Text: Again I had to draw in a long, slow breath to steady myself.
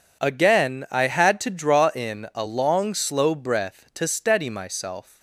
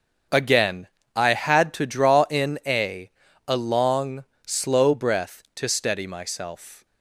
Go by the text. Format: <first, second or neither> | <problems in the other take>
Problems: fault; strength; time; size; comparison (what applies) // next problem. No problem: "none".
first | starts louder than the rest; until 1.5 s; 6.5 dB // pauses between "Again" and "I"; slight; at 0.8 s; 0.26 s long // says "a" twice; at 3.4 s